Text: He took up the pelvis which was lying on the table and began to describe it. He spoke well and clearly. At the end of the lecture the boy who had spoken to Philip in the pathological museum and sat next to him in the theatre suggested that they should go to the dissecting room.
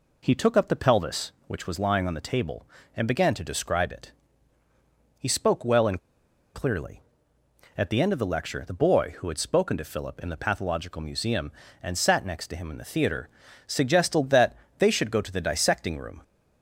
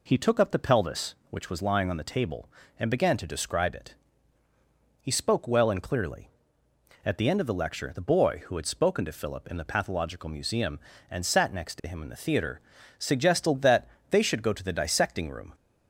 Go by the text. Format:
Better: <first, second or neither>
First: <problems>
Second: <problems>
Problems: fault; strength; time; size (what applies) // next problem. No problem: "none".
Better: second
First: pauses between "and" and "clearly"; noticeable; at 5.9 s; 0.55 s long // pauses between "theatre" and "suggested"; at 13.2 s; 0.40 s long // pauses between "that" and "they"; slight; at 14.5 s; 0.24 s long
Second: pauses between "theatre" and "suggested"; at 12.5 s; 0.40 s long // pauses between "that" and "they"; slight; at 13.8 s; 0.24 s long